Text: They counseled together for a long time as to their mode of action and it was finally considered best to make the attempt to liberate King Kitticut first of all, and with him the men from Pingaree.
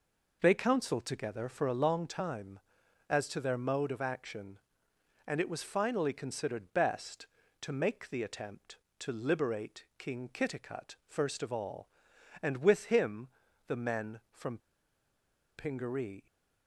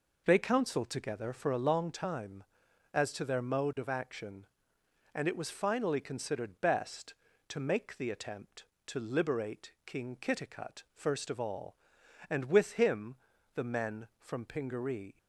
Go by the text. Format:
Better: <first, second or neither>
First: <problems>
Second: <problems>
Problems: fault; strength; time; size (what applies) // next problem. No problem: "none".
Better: second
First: pauses between "him" and "the"; at 13.2 s; 0.40 s long // pauses between "from" and "Pingaree"; at 14.5 s; 0.99 s long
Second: pauses between "him" and "the"; at 13.1 s; 0.40 s long